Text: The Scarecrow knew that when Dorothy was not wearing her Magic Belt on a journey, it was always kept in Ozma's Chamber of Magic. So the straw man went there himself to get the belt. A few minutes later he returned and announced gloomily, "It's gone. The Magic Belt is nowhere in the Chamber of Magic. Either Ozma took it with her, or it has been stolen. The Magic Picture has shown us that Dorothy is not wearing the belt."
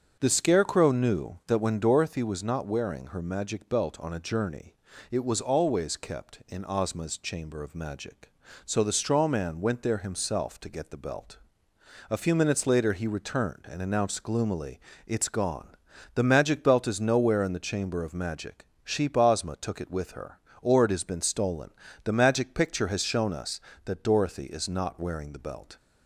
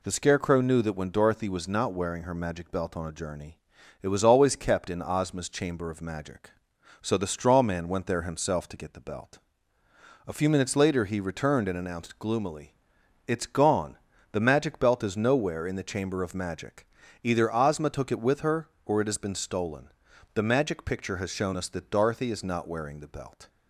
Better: second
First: starts louder than the rest; strong; until 1.2 s; 7 dB // says "Sheep" for "Either"; at 18.8 s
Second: none

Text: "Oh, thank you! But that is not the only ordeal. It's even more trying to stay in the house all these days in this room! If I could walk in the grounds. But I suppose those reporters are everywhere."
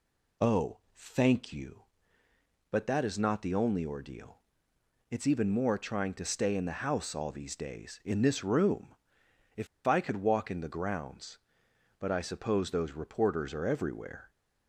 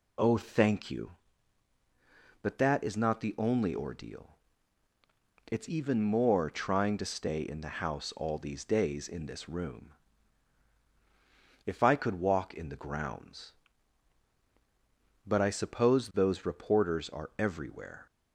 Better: second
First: pauses between "If" and "I"; slight; at 9.6 s; 0.20 s long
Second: none

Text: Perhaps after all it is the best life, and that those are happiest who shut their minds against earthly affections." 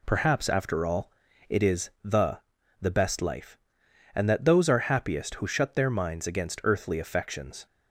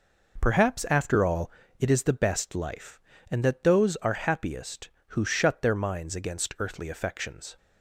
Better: second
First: pauses between "all" and "it"; at 1.0 s; 0.38 s long // says "the" twice; at 2.8 s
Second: pauses between "all" and "it"; slight; at 1.5 s; 0.28 s long

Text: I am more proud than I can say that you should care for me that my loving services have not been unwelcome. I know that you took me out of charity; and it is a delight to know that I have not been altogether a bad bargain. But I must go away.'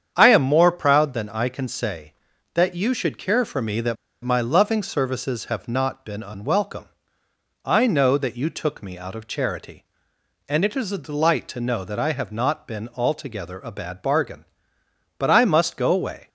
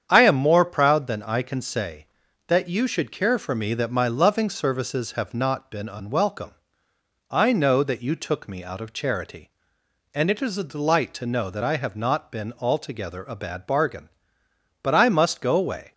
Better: second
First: starts louder than the rest; strong; until 1.1 s; 8 dB // pauses between "that" and "my"; slight; at 3.9 s; 0.28 s long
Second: starts louder than the rest; strong; until 1.0 s; 8 dB

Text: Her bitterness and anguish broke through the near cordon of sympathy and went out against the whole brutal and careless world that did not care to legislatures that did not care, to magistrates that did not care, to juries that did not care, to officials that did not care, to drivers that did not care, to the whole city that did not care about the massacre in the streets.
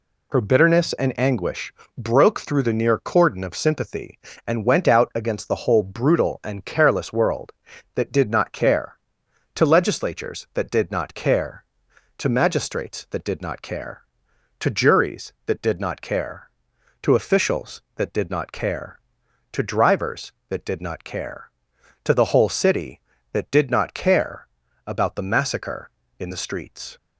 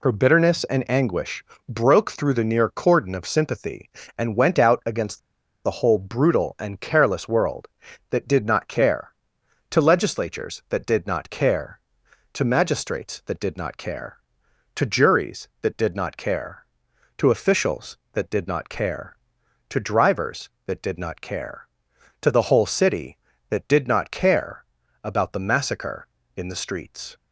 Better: first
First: pauses between "anguish" and "broke"; slight; at 1.7 s; 0.24 s long // pauses between "care" and "about"; at 24.4 s; 0.40 s long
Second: pauses between "anguish" and "broke"; slight; at 1.4 s; 0.24 s long // pauses between "against" and "the"; noticeable; at 5.1 s; 0.46 s long // pauses between "care" and "about"; at 24.6 s; 0.40 s long

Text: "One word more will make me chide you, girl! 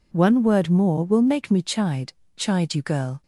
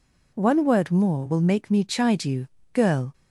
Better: second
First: says "chide" twice; at 2.3 s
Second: none

